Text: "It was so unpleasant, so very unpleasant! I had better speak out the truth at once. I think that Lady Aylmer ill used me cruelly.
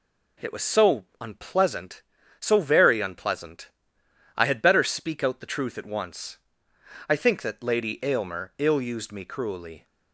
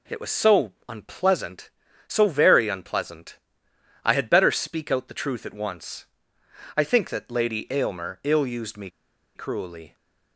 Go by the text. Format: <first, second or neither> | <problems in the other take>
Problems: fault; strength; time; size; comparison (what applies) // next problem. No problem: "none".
first | pauses between "so" and "unpleasant"; slight; at 0.7 s; 0.16 s long; slight in the first // pauses between "me" and "cruelly"; noticeable; at 8.8 s; 0.46 s long